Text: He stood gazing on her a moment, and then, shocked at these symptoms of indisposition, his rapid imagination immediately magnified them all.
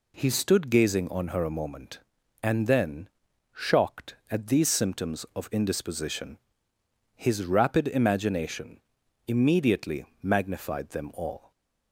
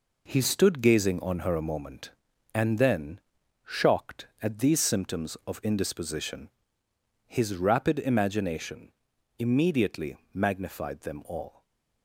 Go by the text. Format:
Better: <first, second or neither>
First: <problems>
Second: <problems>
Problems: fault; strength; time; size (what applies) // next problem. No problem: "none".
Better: first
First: pauses between "imagination" and "immediately"; noticeable; at 8.7 s; 0.48 s long // pauses between "immediately" and "magnified"; slight; at 10.0 s; 0.18 s long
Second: gets quieter; throughout; 6.5 dB // pauses between "imagination" and "immediately"; noticeable; at 8.9 s; 0.48 s long // pauses between "immediately" and "magnified"; slight; at 10.1 s; 0.18 s long // stays silent after the last word; slight; from 11.4 s on; 0.6 s long